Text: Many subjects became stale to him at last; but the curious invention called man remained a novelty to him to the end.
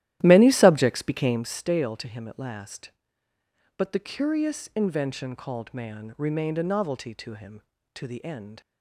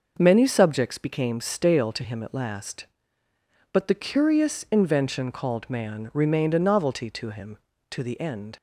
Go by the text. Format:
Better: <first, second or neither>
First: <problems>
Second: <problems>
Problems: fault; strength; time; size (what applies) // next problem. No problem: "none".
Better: second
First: starts louder than the rest; strong; until 1.6 s; 13.5 dB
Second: none